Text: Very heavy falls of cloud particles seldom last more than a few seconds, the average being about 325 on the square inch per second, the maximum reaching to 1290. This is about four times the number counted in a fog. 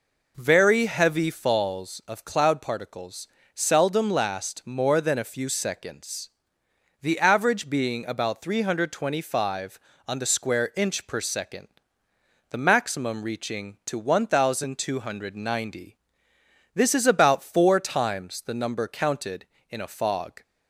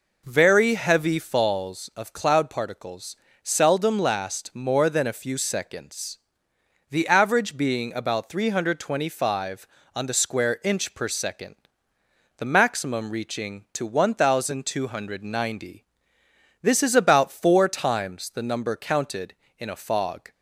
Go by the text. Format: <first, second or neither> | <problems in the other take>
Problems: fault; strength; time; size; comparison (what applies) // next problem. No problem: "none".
neither | pauses between "particles" and "seldom"; slight; the same in both